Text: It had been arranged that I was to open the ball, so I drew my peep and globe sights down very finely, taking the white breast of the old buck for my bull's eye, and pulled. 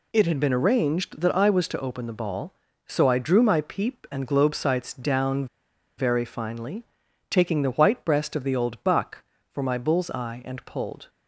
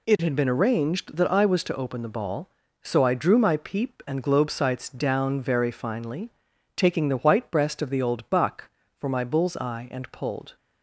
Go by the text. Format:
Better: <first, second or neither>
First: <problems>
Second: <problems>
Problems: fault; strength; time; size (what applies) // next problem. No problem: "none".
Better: second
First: pauses between "down" and "very"; noticeable; at 5.4 s; 0.52 s long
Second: none